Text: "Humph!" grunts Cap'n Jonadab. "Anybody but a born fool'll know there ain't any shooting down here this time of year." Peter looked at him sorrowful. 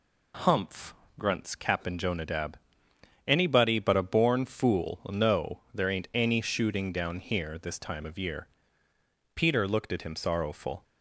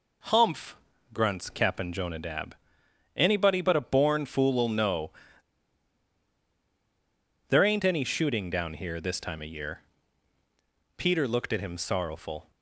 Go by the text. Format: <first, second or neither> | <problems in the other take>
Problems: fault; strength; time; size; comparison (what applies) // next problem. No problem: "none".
first | pauses between "know" and "there"; strong; at 5.1 s; 2.3 s long